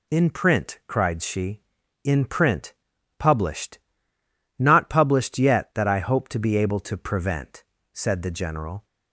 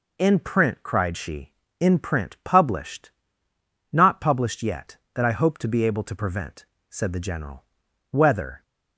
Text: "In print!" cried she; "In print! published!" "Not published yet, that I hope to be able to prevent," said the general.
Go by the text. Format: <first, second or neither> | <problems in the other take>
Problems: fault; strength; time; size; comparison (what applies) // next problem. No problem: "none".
first | goes on to say "Whether"; from 8.1 s on; 0.52 s long